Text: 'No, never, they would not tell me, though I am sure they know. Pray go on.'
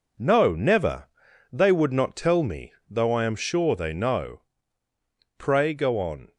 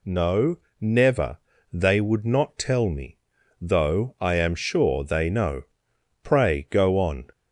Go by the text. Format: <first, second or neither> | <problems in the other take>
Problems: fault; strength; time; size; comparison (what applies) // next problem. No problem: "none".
second | gets quieter; strong; throughout; 7.5 dB